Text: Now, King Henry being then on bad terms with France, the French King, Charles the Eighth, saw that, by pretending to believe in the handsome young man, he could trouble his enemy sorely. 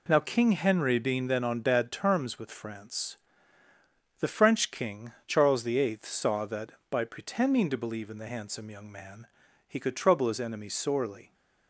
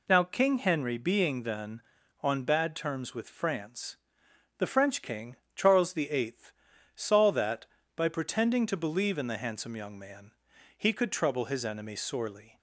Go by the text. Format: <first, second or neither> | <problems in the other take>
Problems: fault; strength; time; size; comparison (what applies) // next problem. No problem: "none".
neither | none